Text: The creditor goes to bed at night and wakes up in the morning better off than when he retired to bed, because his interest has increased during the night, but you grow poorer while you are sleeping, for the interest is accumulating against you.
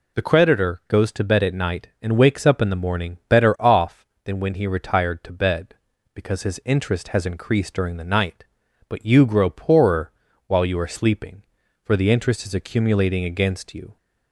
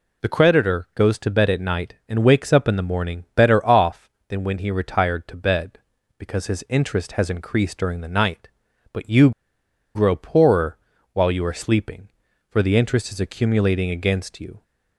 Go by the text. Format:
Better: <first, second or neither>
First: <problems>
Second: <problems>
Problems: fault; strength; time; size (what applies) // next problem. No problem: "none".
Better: first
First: pauses between "poorer" and "while"; slight; at 10.1 s; 0.36 s long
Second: pauses between "you" and "grow"; noticeable; at 9.3 s; 0.64 s long // pauses between "poorer" and "while"; slight; at 10.7 s; 0.36 s long